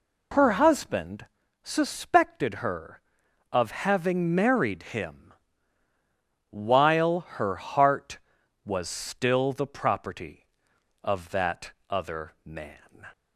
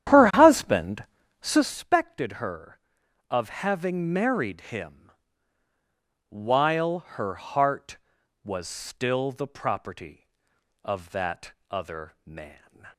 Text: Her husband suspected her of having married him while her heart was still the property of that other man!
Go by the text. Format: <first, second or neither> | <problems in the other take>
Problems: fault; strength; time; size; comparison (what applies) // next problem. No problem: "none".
first | starts louder than the rest; strong; until 1.8 s; 10.5 dB // pauses between "husband" and "suspected"; slight; at 1.0 s; 0.36 s long; slight in the first // pauses between "him" and "while"; at 5.1 s; 1.1 s long; also in the first // pauses between "while" and "her"; slight; at 6.9 s; 0.16 s long; slight in the first // pauses between "that" and "other"; slight; at 11.5 s; 0.18 s long; slight in the first